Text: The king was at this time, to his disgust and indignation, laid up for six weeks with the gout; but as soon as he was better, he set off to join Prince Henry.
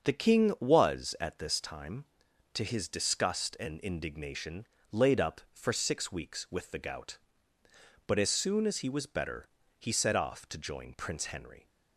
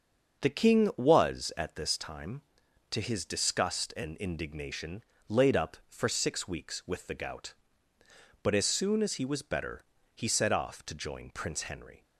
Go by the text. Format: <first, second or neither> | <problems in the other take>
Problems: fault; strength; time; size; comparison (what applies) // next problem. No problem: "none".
neither | starts louder than the rest; the same in both